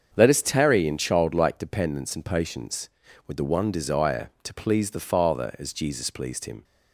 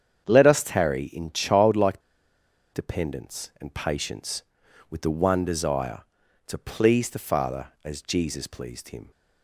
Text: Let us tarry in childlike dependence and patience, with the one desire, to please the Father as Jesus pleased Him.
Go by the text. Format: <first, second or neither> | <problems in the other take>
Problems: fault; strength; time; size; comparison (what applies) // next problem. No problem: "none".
first | starts louder than the rest; strong; until 1.3 s; 8 dB; also in the first // pauses between "childlike" and "dependence"; noticeable; at 2.0 s; 0.73 s long